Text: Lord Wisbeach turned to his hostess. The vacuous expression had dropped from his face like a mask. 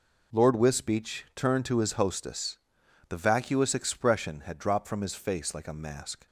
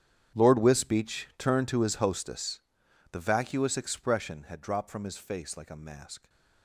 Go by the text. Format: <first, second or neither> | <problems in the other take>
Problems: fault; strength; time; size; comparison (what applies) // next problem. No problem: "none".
first | gets quieter; strong; throughout; 18.5 dB